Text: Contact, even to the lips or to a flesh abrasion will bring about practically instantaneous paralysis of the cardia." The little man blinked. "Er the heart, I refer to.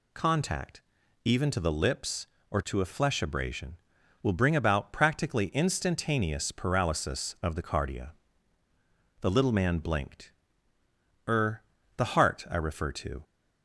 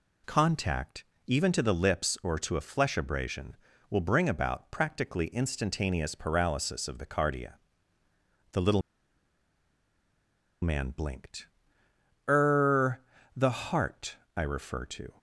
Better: first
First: pauses between "Er" and "the"; slight; at 11.6 s; 0.36 s long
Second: pauses between "little" and "man"; strong; at 8.8 s; 1.8 s long // pauses between "Er" and "the"; slight; at 12.9 s; 0.36 s long

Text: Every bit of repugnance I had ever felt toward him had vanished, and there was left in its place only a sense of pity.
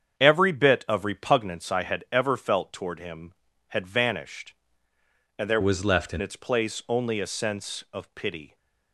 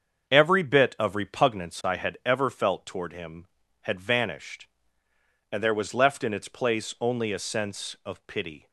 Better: second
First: starts louder than the rest; strong; until 1.2 s; 7.5 dB // changes voice from "was" to "in"; from 5.6 to 6.2 s; 0.6 s long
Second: starts louder than the rest; until 1.3 s; 7 dB

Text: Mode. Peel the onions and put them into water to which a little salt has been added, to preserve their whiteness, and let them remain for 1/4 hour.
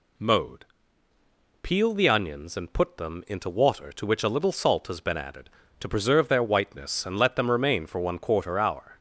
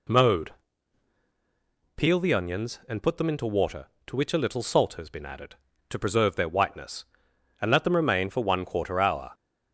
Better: neither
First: none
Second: none

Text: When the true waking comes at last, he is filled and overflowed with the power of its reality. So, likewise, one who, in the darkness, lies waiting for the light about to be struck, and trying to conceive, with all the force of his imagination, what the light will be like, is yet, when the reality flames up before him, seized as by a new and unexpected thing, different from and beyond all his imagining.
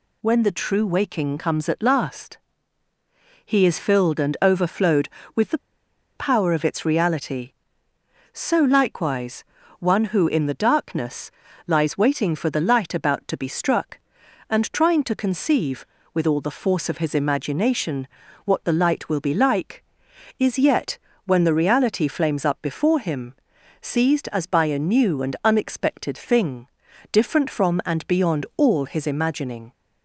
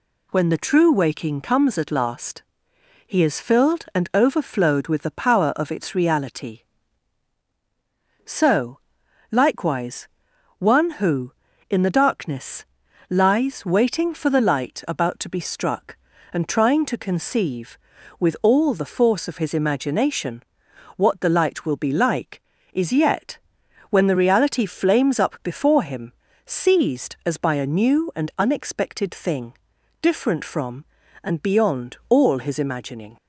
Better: second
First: pauses between "the" and "power"; noticeable; at 5.5 s; 0.58 s long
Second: none

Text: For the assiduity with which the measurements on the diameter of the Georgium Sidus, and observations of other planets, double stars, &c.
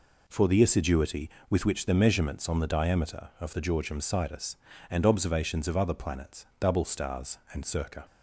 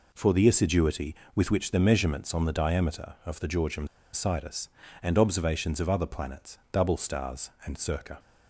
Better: first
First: none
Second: pauses between "Georgium" and "Sidus"; slight; at 3.8 s; 0.26 s long

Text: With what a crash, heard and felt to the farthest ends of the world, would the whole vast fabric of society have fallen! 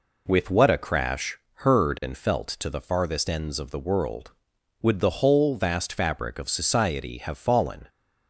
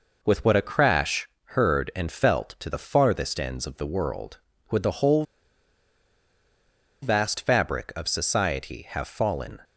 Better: first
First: none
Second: pauses between "whole" and "vast"; strong; at 5.2 s; 1.7 s long

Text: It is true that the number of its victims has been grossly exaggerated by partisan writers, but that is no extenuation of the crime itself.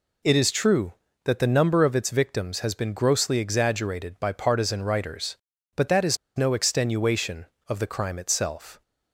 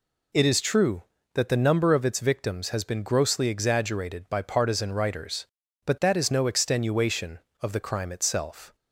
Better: second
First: pauses between "is" and "no"; slight; at 6.1 s; 0.19 s long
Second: none

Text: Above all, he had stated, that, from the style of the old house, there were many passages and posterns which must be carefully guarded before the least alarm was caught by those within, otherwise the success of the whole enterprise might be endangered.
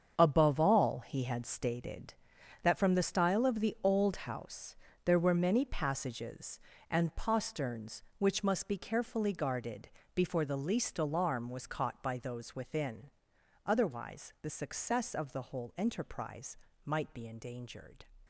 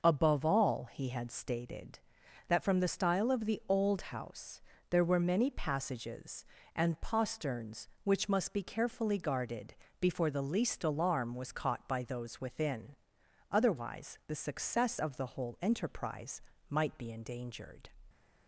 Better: second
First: gets quieter; strong; throughout; 10.5 dB // pauses between "guarded" and "before"; slight; at 9.8 s; 0.24 s long // pauses between "enterprise" and "might"; slight; at 16.5 s; 0.28 s long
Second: pauses between "guarded" and "before"; slight; at 9.7 s; 0.24 s long // pauses between "enterprise" and "might"; slight; at 16.4 s; 0.28 s long

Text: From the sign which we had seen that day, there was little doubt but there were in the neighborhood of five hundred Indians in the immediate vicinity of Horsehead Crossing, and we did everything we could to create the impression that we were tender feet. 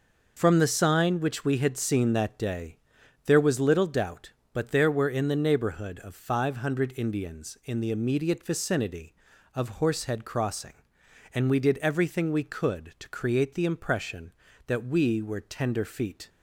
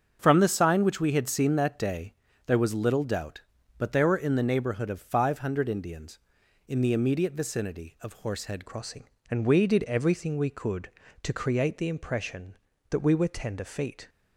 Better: first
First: none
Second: starts louder than the rest; strong; until 1.2 s; 7 dB // changes voice at "Crossing"; from 8.6 s on; 5.4 s long

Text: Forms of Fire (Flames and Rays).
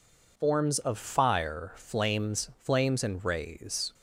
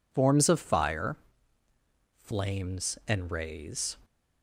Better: second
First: says "Flames" twice; at 2.5 s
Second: none

